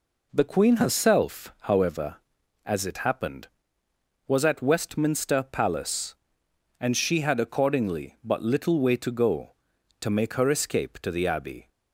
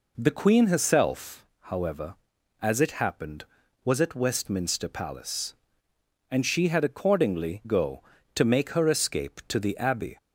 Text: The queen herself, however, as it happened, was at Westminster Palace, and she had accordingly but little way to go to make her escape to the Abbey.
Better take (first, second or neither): first